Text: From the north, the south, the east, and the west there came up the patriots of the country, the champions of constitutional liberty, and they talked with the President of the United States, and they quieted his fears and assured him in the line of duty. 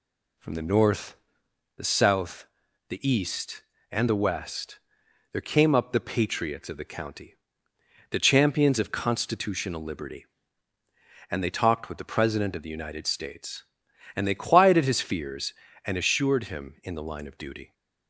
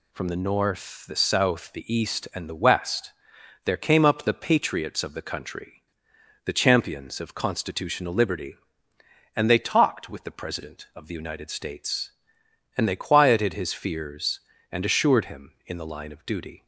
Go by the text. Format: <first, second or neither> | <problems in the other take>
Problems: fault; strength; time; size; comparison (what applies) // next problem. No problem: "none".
second | pauses between "west" and "there"; noticeable; at 4.7 s; 0.54 s long; noticeable in the second // says "county" for "country"; at 6.8 s